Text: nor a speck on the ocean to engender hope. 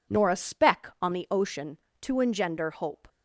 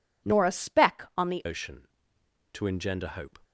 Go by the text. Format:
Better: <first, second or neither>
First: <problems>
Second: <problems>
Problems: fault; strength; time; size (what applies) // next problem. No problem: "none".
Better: first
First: none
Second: changes voice at "ocean"; from 1.4 s on; 1.9 s long